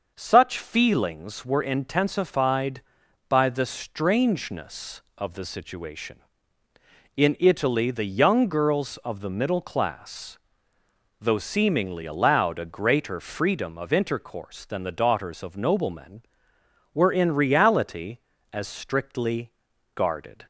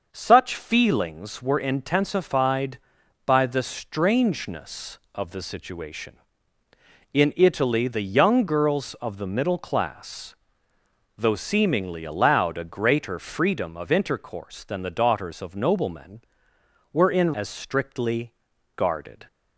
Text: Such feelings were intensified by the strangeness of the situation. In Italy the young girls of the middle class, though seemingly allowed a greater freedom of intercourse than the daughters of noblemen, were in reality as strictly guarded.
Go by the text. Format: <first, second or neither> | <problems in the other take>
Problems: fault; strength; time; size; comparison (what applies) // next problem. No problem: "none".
first | starts louder than the rest; noticeable; until 1.1 s; 6 dB; noticeable in the first // skips "reality"; at 17.3 s // pauses between "strictly" and "guarded"; at 18.3 s; 0.42 s long; also in the first